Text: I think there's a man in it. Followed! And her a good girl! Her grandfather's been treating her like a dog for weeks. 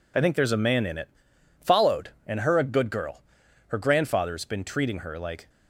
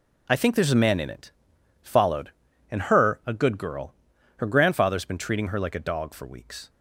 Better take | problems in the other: second | stops before "a dog for weeks"; at 5.4 s

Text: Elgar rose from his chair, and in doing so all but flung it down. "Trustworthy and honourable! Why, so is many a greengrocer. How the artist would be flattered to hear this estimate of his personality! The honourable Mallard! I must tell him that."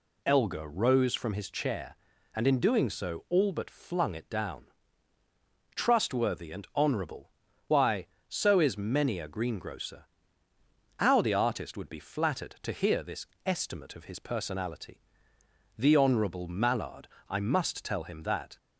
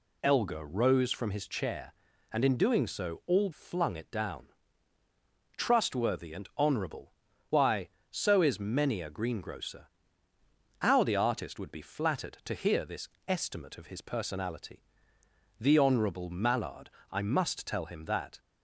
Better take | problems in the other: first | skips "but"; at 3.5 s // pauses between "this" and "estimate"; slight; at 13.0 s; 0.20 s long; slight in the first

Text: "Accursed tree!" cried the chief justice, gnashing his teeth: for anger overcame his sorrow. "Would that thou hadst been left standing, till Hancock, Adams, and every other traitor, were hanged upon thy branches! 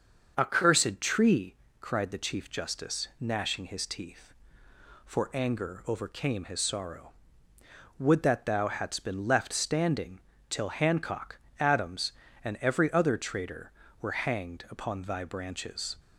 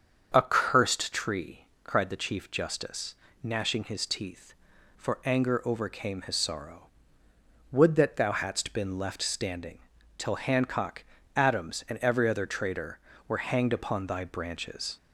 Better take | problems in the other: neither | starts louder than the rest; the same in both

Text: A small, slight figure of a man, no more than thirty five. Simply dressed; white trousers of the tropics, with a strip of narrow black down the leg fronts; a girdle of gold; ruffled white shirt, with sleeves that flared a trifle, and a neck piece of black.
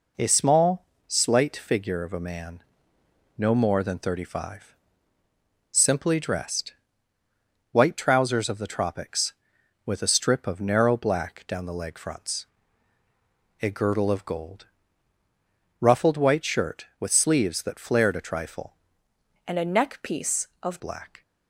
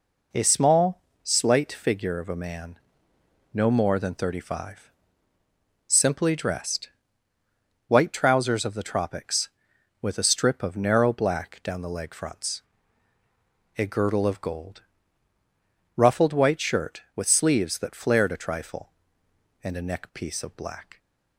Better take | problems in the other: second | changes voice from "and" to "of"; from 19.4 to 20.8 s; 1.4 s long

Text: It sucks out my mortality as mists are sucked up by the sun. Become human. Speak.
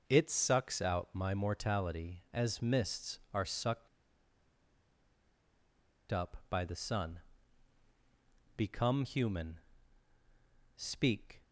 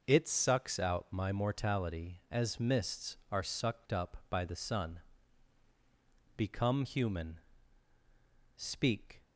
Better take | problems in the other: second | pauses between "sucked" and "up"; strong; at 3.8 s; 2.2 s long

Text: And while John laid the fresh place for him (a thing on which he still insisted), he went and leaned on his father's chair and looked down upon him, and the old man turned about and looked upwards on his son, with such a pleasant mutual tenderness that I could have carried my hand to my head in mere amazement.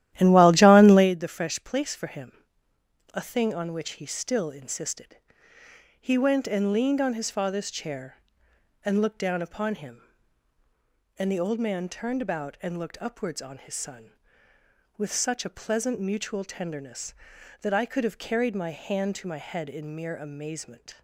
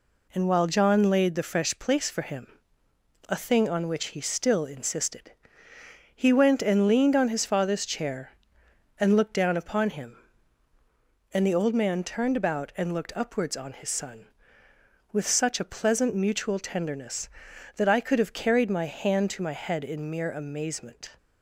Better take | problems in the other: second | starts louder than the rest; strong; until 1.1 s; 13 dB

